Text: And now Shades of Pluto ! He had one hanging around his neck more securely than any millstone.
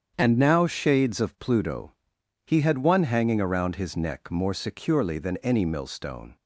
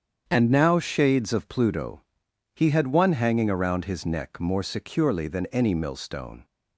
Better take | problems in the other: neither | starts louder than the rest; strong; the same in both

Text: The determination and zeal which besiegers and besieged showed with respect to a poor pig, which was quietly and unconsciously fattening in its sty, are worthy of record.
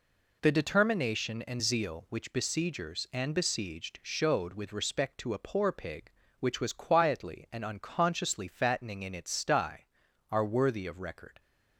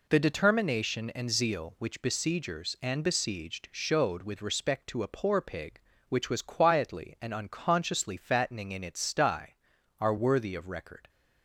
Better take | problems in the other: neither | none

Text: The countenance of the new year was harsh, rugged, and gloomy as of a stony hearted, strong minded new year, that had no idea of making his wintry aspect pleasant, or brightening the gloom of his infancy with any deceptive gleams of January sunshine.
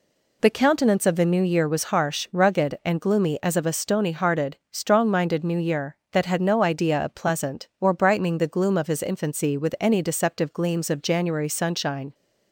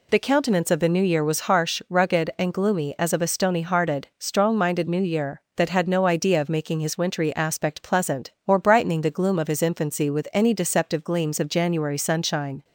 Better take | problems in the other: second | skips "making his wintry aspect"; at 7.1 s

